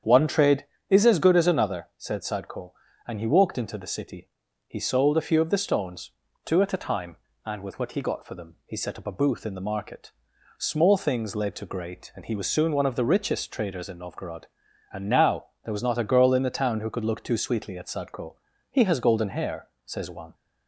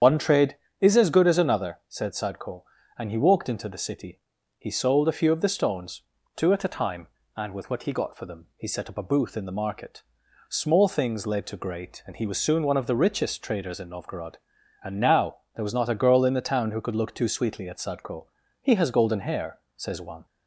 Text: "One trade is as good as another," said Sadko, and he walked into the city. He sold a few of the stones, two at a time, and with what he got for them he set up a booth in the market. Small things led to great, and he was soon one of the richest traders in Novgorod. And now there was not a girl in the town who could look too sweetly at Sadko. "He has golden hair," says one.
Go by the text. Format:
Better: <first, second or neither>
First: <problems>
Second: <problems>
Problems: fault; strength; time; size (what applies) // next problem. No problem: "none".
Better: first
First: starts louder than the rest; strong; until 1.2 s; 8 dB // pauses between "now" and "there"; slight; at 15.4 s; 0.18 s long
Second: loses the start of "One"; at 0.0 s; 70 ms // starts louder than the rest; strong; until 1.2 s; 8 dB // pauses between "now" and "there"; slight; at 15.3 s; 0.18 s long